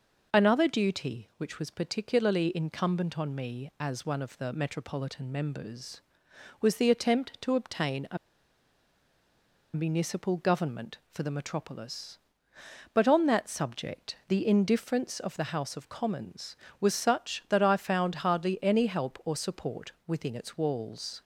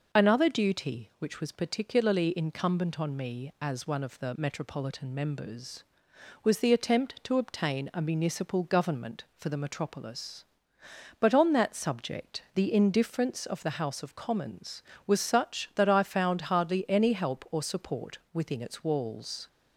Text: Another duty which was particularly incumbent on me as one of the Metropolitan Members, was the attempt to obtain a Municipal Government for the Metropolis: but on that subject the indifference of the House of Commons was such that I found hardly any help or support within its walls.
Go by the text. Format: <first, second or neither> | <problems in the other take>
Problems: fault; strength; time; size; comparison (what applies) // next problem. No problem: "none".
second | pauses between "a" and "Municipal"; strong; at 8.1 s; 1.5 s long // pauses between "support" and "within"; slight; at 19.9 s; 0.16 s long; slight in the second